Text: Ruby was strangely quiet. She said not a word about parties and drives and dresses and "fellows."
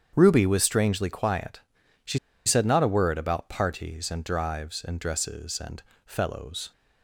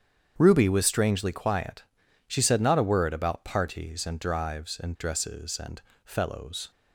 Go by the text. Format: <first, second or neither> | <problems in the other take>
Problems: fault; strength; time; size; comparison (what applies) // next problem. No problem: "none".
second | starts louder than the rest; strong; until 1.1 s; 8 dB; strong in the second // pauses between "She" and "said"; slight; at 2.1 s; 0.28 s long // pauses between "and" and "fellows"; slight; at 5.8 s; 0.24 s long; slight in the second